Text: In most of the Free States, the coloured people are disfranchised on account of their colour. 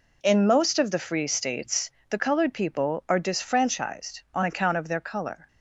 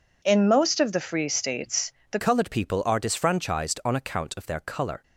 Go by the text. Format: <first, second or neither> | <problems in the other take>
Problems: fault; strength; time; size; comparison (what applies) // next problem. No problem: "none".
first | changes voice at "coloured"; from 2.1 s on; 2.9 s long